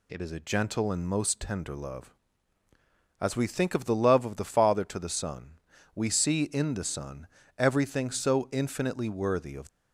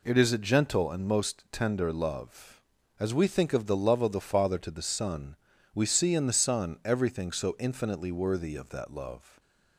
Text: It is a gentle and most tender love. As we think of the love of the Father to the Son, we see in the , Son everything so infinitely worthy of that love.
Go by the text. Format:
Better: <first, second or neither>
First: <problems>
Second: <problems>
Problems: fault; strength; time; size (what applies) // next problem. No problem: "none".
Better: second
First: pauses between "Son" and "everything"; slight; at 7.2 s; 0.30 s long // stops before "that love"; at 9.6 s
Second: none